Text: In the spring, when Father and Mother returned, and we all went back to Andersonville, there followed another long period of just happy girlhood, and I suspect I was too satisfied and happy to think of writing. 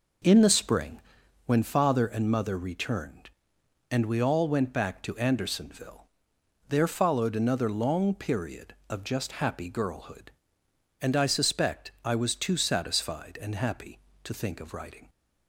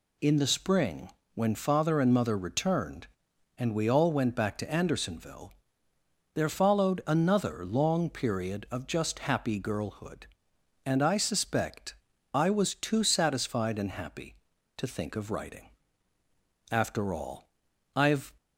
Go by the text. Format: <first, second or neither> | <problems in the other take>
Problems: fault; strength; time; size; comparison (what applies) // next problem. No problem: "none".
first | pauses between "suspect" and "I"; slight; at 11.9 s; 0.36 s long // goes on to say "After all I've"; from 16.7 s on; 1.6 s long